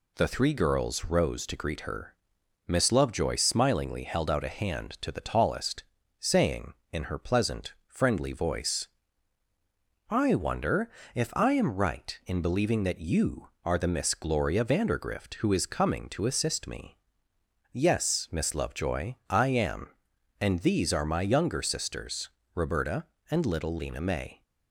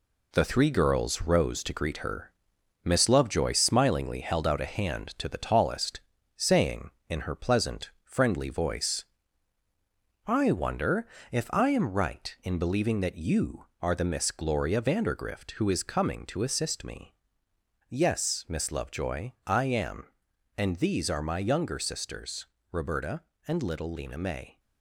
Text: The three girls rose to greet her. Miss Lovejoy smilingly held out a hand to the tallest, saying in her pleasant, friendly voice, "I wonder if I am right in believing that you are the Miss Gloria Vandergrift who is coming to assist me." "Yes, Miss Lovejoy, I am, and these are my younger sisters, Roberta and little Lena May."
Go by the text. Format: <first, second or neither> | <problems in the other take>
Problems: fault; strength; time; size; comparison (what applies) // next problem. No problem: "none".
first | gets quieter; noticeable; throughout; 5.5 dB // pauses between "wonder" and "if"; slight; at 11.0 s; 0.24 s long; slight in the first